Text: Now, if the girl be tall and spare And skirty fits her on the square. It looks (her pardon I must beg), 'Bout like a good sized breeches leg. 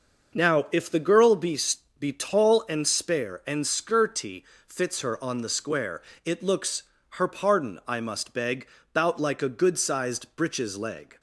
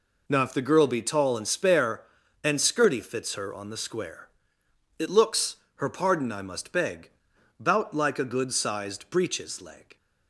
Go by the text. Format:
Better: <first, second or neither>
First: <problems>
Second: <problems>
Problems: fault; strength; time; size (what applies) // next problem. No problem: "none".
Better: second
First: says "be" twice; at 1.9 s // pauses between "skirty" and "fits"; slight; at 4.4 s; 0.24 s long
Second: none